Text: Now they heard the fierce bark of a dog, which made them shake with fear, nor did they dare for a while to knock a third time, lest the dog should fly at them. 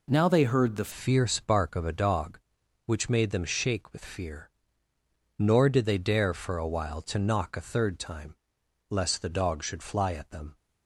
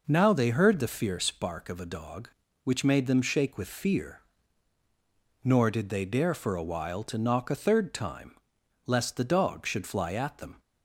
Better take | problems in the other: second | changes voice at "fierce"; from 0.9 s on; 9.6 s long

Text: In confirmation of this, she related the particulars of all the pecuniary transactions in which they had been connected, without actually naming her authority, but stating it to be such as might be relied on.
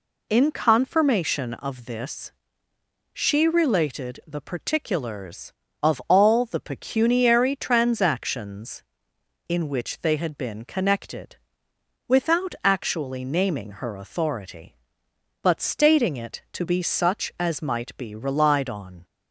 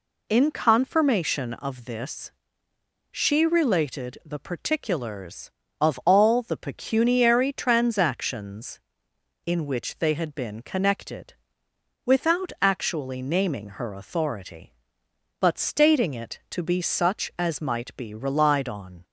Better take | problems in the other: neither | none

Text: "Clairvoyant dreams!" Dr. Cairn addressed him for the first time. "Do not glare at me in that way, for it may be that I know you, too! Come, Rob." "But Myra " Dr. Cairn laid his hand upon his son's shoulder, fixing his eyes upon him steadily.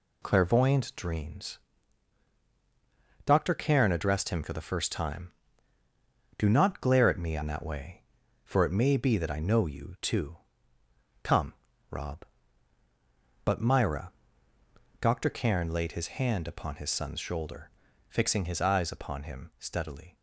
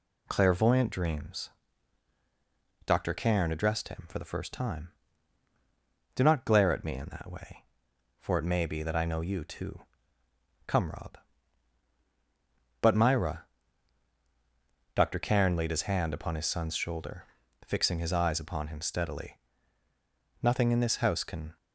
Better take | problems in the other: first | goes on to say "Nothing in this house can"; noticeable; from 20.4 s on; 1.1 s long

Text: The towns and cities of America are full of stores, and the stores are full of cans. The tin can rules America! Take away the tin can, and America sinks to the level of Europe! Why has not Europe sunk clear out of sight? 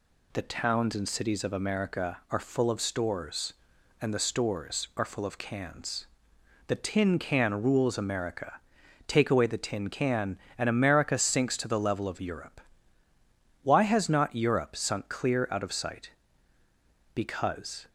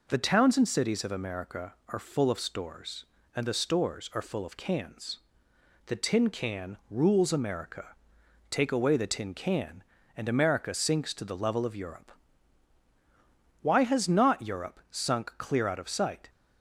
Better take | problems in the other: second | goes on to say "Because"; noticeable; from 17.1 s on; 0.72 s long

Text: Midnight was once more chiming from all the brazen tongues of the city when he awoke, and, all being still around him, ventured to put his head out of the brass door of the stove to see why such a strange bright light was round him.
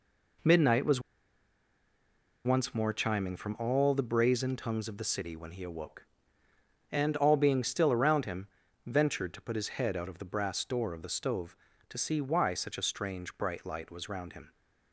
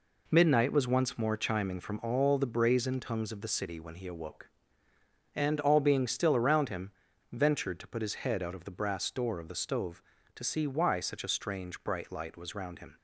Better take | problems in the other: second | pauses between "was" and "once"; strong; at 1.0 s; 1.4 s long

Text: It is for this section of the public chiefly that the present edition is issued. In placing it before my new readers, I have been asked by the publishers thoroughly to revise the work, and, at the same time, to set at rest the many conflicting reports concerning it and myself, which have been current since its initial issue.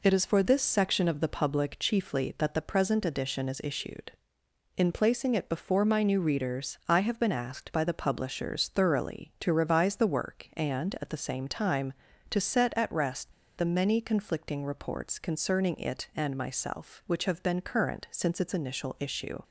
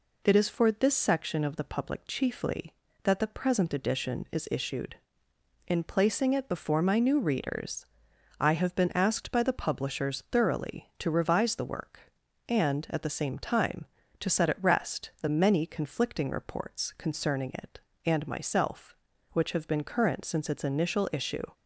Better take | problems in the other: second | pauses between "rest" and "the"; slight; at 13.3 s; 0.26 s long

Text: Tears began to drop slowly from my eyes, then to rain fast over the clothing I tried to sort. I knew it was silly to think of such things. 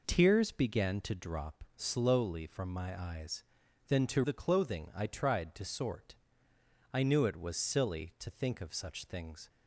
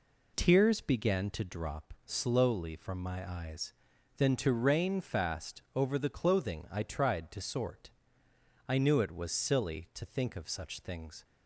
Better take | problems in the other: second | skips "rain fast over"; at 4.2 s

